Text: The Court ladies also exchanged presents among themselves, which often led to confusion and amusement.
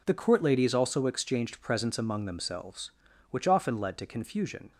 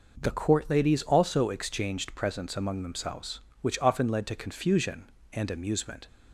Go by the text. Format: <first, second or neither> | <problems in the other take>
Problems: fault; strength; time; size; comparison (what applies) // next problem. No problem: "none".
second | stops before "and amusement"; at 4.7 s